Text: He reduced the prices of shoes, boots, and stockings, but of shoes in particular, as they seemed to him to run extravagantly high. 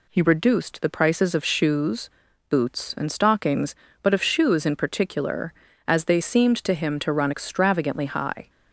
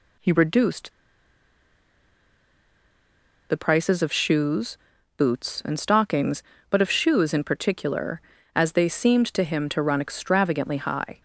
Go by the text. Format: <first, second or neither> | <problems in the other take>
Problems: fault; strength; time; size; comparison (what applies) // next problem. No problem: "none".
first | pauses between "reduced" and "the"; strong; at 0.9 s; 2.5 s long